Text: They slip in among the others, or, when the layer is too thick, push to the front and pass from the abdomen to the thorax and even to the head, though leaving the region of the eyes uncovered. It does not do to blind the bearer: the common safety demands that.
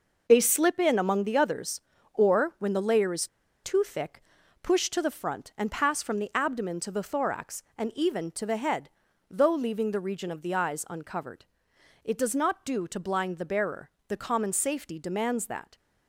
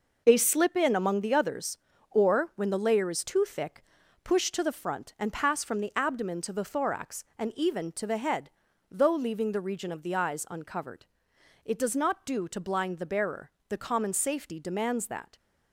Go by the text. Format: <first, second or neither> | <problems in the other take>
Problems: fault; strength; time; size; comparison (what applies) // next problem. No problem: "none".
second | pauses between "is" and "too"; at 3.2 s; 0.36 s long